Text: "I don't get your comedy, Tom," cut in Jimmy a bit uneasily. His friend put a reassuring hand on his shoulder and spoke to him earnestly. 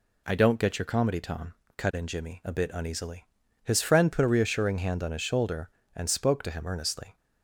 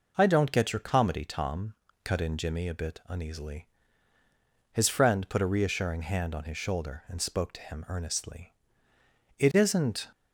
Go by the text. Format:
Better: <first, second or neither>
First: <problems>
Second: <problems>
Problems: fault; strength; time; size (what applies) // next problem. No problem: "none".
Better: first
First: none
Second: goes on to say "It isn't"; noticeable; from 9.3 s on; 0.68 s long